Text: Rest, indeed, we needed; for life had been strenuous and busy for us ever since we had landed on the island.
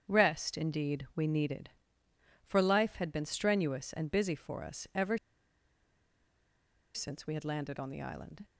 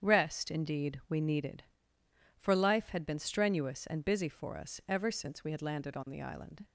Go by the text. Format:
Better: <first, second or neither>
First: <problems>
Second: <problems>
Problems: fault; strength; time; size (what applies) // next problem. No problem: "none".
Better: second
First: starts louder than the rest; strong; until 1.1 s; 8 dB // pauses between "ever" and "since"; strong; at 5.1 s; 1.7 s long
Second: starts louder than the rest; strong; until 1.0 s; 8 dB